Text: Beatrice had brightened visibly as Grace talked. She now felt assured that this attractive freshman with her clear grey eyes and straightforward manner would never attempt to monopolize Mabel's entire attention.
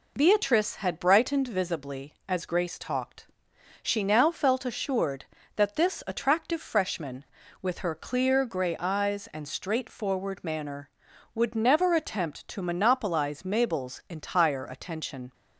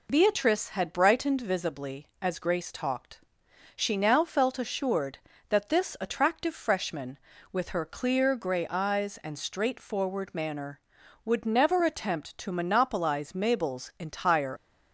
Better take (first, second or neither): first